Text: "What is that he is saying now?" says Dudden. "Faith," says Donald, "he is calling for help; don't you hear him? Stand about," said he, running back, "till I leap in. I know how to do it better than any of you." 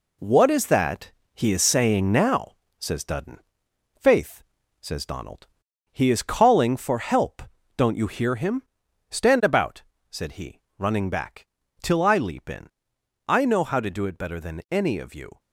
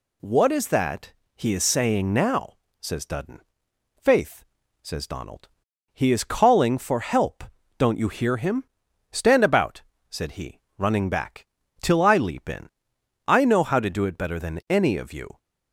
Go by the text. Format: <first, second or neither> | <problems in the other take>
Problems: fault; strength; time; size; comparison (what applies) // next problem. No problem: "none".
second | gets quieter; throughout; 6 dB // pauses between "that" and "he"; slight; at 1.1 s; 0.22 s long; slight in the second